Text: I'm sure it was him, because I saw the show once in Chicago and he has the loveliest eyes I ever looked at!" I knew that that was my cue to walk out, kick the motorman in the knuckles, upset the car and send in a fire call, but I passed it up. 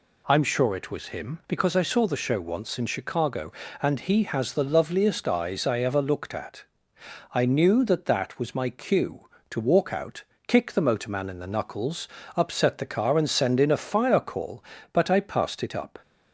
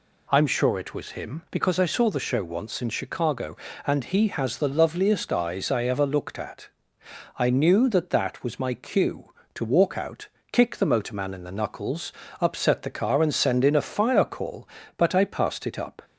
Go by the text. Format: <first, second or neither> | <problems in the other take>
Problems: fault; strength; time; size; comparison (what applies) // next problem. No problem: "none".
neither | none